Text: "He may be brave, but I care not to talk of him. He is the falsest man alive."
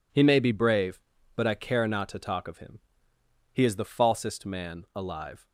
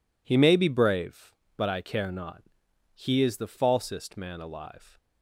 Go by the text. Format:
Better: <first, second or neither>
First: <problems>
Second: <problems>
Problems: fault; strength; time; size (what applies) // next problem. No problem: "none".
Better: first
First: none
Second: skips "to talk of him"; at 2.6 s